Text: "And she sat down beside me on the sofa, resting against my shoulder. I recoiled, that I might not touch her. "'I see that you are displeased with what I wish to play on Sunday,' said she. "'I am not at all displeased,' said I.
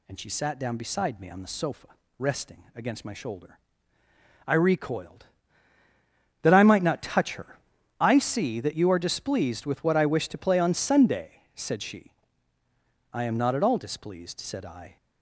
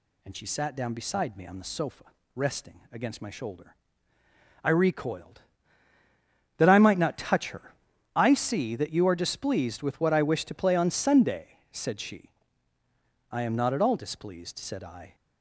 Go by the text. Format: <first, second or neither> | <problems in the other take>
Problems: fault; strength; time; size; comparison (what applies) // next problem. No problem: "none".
neither | none